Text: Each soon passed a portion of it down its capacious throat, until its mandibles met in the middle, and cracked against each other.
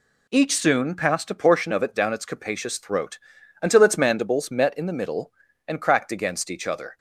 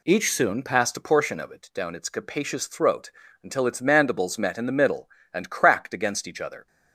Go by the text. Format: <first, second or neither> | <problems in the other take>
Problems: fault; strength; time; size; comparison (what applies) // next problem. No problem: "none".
neither | none